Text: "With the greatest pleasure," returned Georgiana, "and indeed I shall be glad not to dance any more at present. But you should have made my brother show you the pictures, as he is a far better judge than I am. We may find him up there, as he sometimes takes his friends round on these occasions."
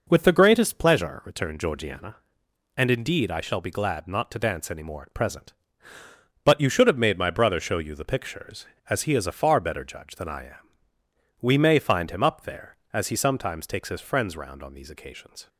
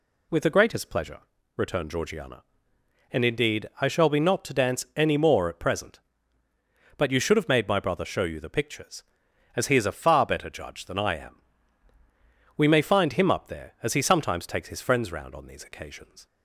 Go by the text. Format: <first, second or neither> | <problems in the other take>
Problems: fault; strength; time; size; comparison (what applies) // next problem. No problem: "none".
first | skips "glad"; at 4.2 s